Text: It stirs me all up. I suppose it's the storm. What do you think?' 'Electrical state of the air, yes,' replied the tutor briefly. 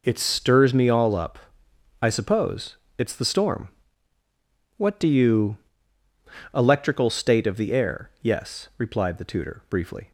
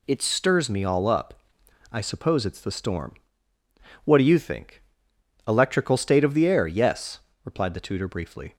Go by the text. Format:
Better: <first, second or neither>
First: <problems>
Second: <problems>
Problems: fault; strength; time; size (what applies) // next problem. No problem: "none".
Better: second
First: pauses between "suppose" and "it's"; slight; at 2.7 s; 0.22 s long // skips "think"; at 6.0 s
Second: none